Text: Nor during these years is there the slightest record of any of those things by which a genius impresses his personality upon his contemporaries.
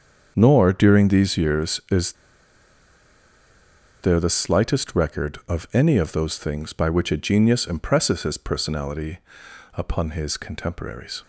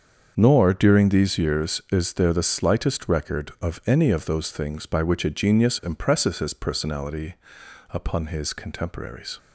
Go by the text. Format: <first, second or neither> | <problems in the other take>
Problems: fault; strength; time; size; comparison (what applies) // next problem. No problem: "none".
second | starts louder than the rest; until 1.3 s; 7 dB; also in the second // pauses between "is" and "there"; strong; at 2.1 s; 1.9 s long // pauses between "personality" and "upon"; noticeable; at 9.1 s; 0.56 s long; noticeable in the second